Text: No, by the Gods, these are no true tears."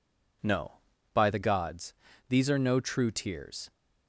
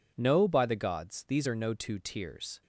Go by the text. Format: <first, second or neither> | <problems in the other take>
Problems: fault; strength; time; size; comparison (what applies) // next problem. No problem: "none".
first | says "two" for "true"; at 1.7 s